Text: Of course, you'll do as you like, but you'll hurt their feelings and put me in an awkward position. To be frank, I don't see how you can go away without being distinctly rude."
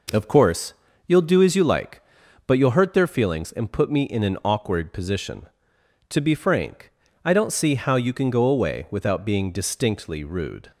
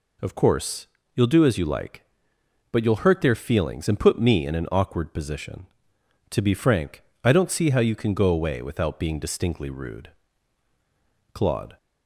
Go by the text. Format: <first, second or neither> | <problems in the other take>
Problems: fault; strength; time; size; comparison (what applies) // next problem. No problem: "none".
first | goes on to say "Claude"; slight; from 11.3 s on; 0.44 s long